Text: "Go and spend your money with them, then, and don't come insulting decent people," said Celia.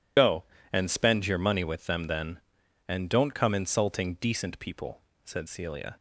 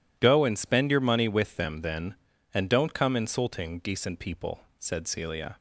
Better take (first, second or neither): second